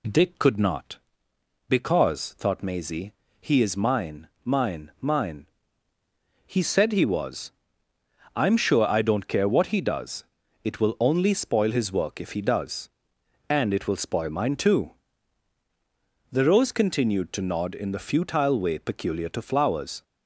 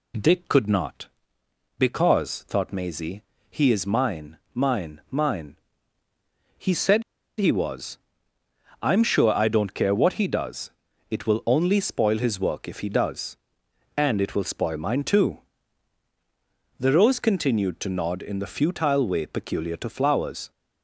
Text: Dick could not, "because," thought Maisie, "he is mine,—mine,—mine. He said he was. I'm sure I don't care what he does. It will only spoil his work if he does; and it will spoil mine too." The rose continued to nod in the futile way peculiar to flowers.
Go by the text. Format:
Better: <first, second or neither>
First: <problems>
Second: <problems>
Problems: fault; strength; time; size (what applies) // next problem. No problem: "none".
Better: first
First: none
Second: pauses between "said" and "he"; slight; at 7.0 s; 0.35 s long